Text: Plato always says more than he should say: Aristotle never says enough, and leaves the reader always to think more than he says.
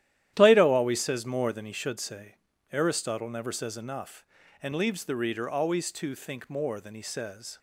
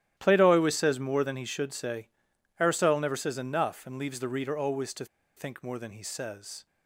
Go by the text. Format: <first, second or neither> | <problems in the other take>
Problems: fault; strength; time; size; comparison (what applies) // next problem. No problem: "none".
first | starts louder than the rest; strong; until 1.1 s; 12.5 dB; strong in the first // pauses between "to" and "think"; slight; at 5.0 s; 0.31 s long